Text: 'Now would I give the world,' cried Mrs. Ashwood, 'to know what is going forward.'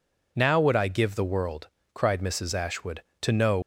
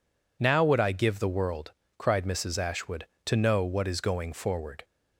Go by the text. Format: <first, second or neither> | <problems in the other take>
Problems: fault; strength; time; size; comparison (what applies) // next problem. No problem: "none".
second | stops before "what is going forward"; at 3.6 s